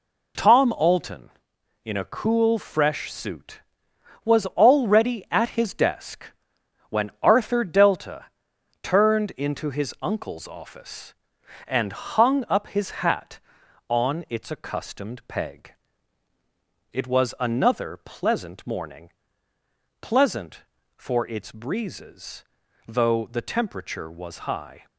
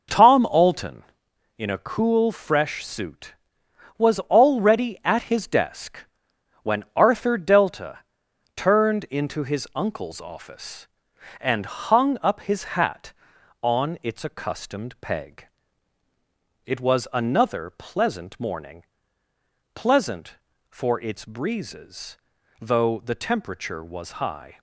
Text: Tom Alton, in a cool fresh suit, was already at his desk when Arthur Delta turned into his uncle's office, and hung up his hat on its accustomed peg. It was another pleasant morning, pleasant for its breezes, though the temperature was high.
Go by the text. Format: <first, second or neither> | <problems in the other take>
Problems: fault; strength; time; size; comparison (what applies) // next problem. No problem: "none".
first | starts louder than the rest; noticeable; until 1.6 s; 5.5 dB // pauses between "desk" and "when"; noticeable; at 5.9 s; 0.64 s long; noticeable in the first // pauses between "Delta" and "turned"; noticeable; at 7.9 s; 0.56 s long; noticeable in the first